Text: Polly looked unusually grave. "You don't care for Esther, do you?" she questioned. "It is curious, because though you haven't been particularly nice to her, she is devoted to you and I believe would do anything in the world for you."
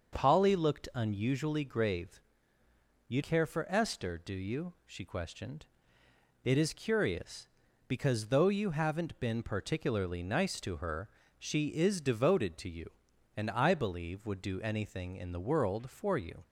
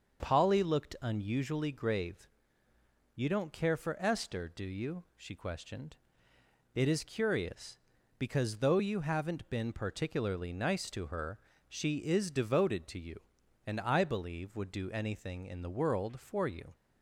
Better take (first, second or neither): second